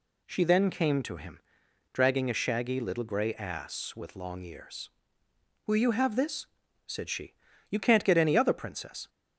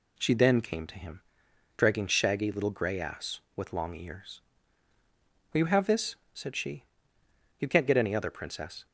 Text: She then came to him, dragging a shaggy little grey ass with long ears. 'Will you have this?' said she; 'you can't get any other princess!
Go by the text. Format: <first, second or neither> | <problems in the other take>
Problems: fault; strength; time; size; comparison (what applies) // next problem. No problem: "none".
first | skips "a"; at 2.0 s